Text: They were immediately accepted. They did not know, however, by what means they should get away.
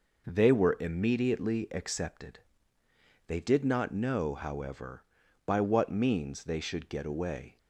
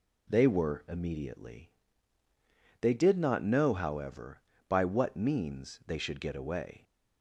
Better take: first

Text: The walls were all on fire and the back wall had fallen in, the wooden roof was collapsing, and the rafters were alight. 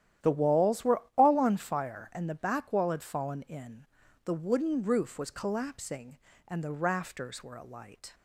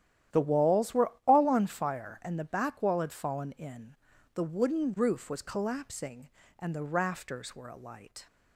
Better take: neither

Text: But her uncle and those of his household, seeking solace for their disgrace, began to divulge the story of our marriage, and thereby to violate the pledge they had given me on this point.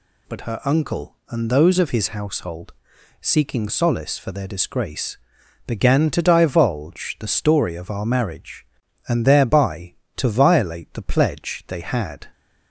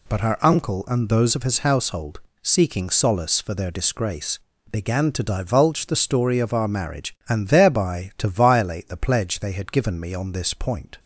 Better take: second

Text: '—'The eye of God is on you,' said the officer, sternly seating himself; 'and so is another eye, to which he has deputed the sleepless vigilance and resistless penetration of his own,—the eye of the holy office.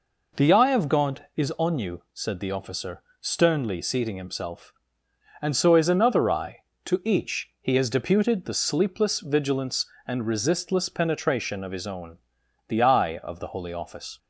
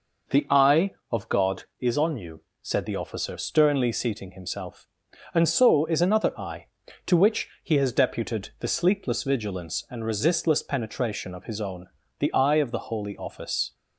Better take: second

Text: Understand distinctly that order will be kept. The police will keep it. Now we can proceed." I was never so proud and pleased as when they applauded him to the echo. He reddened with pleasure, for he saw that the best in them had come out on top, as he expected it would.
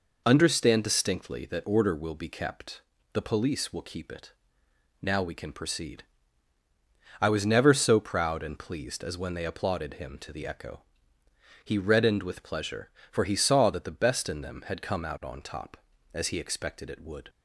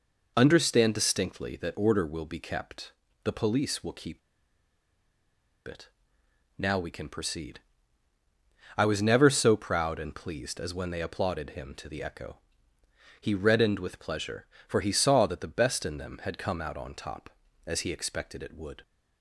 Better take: first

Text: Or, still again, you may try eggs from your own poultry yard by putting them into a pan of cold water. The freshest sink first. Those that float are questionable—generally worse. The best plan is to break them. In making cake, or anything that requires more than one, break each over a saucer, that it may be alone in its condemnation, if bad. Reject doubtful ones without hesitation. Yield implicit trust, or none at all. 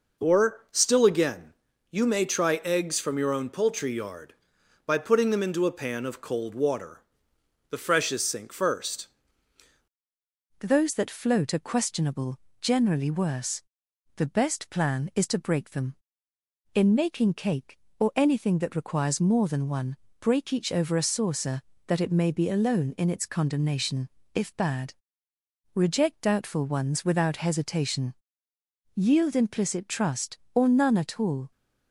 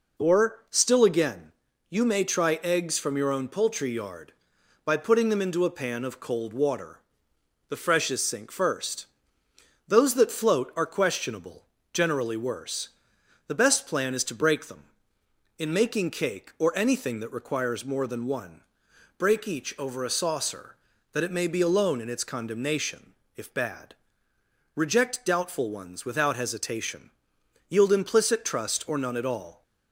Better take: second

